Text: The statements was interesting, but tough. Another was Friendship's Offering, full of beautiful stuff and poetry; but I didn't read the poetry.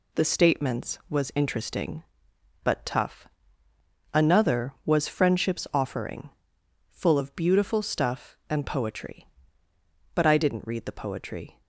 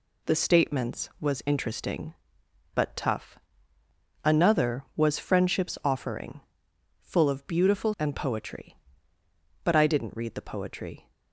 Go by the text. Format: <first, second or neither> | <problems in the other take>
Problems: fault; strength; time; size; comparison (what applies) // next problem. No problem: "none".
first | skips "stuff"; at 7.9 s